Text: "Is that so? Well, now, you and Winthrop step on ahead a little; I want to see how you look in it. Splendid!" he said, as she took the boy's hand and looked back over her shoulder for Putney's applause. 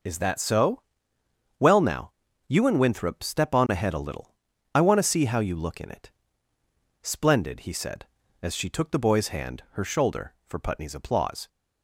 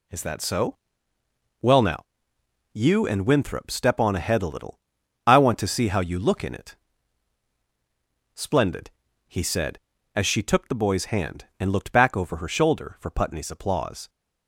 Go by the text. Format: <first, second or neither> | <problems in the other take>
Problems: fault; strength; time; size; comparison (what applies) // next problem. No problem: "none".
second | skips "and looked back over"; at 9.6 s